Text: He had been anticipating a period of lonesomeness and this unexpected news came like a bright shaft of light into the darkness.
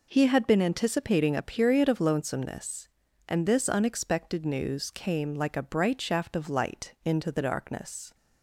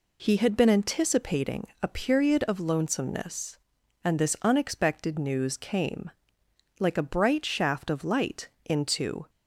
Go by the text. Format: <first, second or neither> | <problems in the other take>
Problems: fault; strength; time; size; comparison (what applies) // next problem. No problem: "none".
first | pauses between "anticipating" and "a"; slight; at 1.6 s; 0.16 s long // pauses between "came" and "like"; noticeable; at 6.0 s; 0.68 s long // pauses between "light" and "into"; slight; at 8.4 s; 0.16 s long // stops before "the darkness"; at 9.2 s